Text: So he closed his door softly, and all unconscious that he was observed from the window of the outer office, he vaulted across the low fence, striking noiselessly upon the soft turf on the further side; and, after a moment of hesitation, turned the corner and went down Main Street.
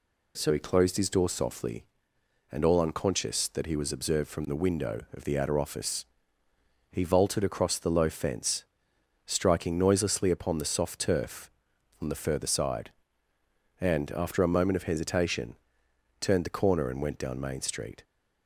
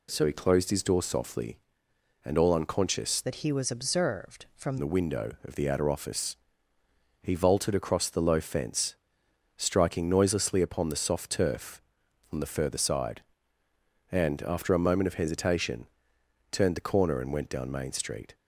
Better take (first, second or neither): first